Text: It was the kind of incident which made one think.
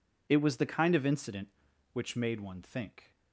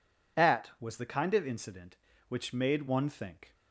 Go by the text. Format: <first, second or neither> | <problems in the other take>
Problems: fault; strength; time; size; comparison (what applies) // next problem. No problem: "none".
first | says "At" for "It"; at 0.3 s